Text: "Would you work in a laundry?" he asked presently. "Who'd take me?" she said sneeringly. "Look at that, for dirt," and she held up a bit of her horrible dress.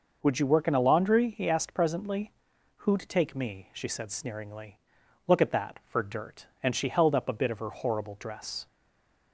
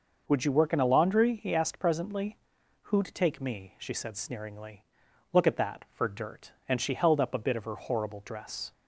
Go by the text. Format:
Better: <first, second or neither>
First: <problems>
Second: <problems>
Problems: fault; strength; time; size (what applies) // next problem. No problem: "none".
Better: second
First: stays silent after the last word; slight; from 8.6 s on; 0.7 s long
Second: none